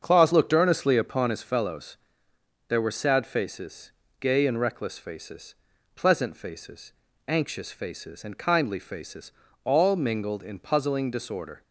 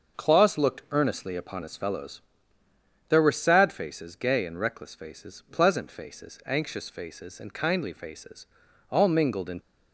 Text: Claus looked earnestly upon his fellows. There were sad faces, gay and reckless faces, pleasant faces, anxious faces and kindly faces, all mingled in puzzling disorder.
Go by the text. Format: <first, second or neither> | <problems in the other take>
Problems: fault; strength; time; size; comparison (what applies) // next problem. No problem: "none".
first | starts louder than the rest; until 1.2 s; 6 dB; also in the first // stops before "puzzling disorder"; at 9.5 s